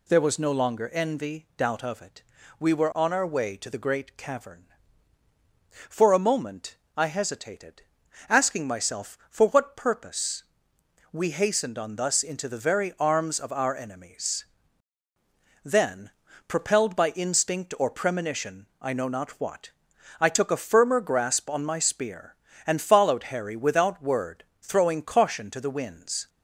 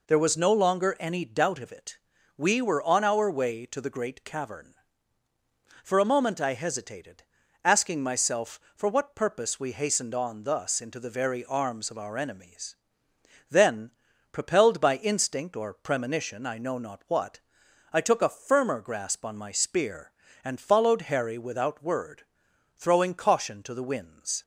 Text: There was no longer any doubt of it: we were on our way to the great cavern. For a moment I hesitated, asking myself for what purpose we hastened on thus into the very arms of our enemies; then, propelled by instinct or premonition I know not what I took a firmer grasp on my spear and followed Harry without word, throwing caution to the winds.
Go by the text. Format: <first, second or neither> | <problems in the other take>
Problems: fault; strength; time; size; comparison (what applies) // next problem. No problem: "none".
second | says "envy" for "any"; at 0.9 s // pauses between "moment" and "I"; slight; at 6.7 s; 0.20 s long // pauses between "purpose" and "we"; noticeable; at 10.4 s; 0.68 s long // pauses between "premonition" and "I"; slight; at 18.6 s; 0.16 s long // pauses between "what" and "I"; noticeable; at 19.6 s; 0.50 s long; noticeable in the second